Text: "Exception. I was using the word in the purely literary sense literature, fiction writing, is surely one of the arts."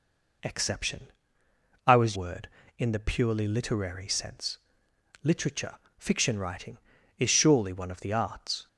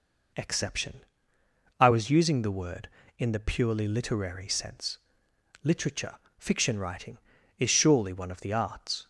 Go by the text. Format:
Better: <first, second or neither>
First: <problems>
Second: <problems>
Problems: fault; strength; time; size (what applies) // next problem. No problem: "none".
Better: second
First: skips "using the"; at 2.1 s // pauses between "sense" and "literature"; noticeable; at 4.5 s; 0.66 s long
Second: pauses between "sense" and "literature"; noticeable; at 4.9 s; 0.66 s long